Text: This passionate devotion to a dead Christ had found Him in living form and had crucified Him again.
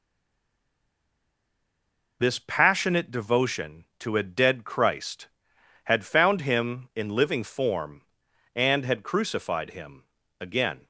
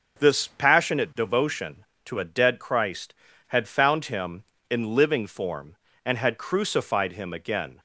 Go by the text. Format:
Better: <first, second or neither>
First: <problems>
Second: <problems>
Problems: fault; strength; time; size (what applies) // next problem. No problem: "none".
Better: second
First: stays silent before the first word; until 2.1 s; 2.1 s long // pauses between "Him" and "again"; slight; at 10.0 s; 0.36 s long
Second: none